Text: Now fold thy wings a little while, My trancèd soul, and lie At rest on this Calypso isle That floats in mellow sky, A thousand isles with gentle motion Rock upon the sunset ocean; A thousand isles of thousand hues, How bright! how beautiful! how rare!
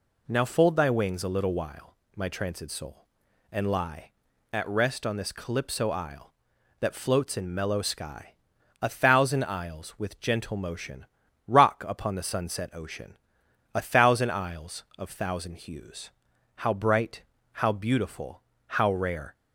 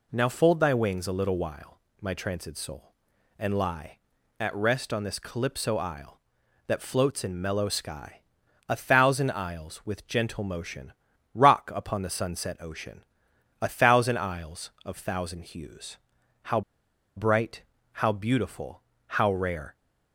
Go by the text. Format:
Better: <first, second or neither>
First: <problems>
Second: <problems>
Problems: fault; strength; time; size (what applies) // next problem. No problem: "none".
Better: first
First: pauses between "motion" and "Rock"; at 11.0 s; 0.42 s long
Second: pauses between "motion" and "Rock"; at 10.9 s; 0.42 s long // pauses between "How" and "bright"; noticeable; at 16.6 s; 0.56 s long